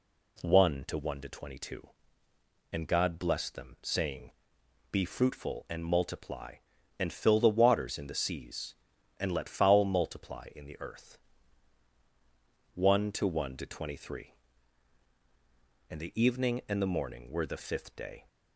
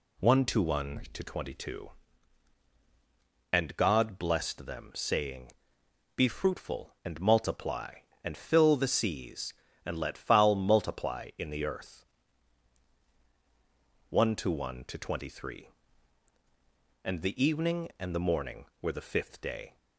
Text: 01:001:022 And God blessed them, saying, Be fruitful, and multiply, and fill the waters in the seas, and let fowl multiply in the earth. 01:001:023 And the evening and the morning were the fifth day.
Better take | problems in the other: first | skips "waters in the"; at 8.8 s

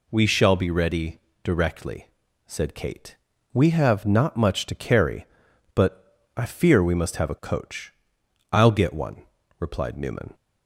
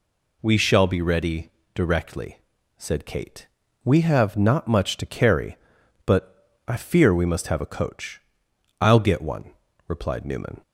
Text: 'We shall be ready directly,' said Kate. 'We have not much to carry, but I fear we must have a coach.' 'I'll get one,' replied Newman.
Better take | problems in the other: neither | pauses between "ready" and "directly"; slight; the same in both // pauses between "but" and "I"; slight; the same in both

